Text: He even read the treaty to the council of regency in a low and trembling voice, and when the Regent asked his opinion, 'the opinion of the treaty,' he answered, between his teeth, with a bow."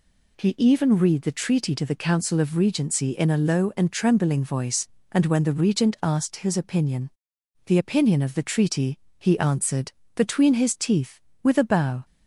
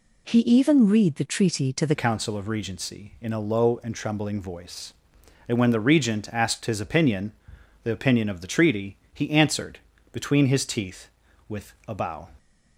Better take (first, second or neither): first